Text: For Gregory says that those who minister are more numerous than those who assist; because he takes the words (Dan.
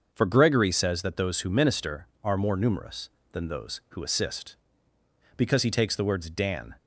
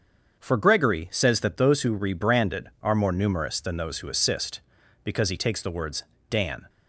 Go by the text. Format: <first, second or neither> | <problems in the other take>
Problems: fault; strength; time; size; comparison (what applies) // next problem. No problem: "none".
first | starts louder than the rest; until 1.4 s; 7 dB; also in the first // says "rebranded" for "minister"; at 1.9 s